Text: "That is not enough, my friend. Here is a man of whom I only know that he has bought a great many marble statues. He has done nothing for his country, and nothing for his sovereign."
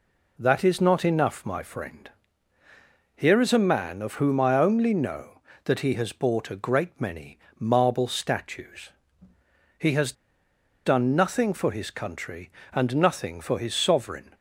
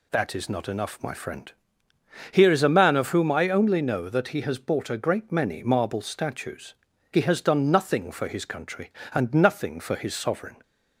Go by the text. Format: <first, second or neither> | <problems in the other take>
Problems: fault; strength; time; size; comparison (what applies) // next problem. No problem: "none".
second | pauses between "many" and "marble"; slight; at 7.3 s; 0.20 s long // pauses between "has" and "done"; noticeable; at 10.1 s; 0.72 s long